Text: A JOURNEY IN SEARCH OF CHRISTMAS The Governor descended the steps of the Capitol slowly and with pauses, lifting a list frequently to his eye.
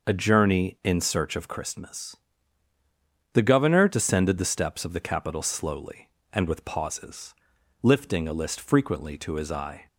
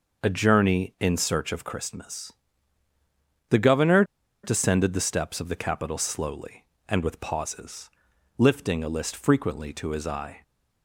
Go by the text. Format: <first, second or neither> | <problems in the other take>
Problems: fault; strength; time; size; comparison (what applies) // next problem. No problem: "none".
first | pauses between "CHRISTMAS" and "The"; at 2.3 s; 1.1 s long; also in the first // pauses between "Governor" and "descended"; at 4.0 s; 0.40 s long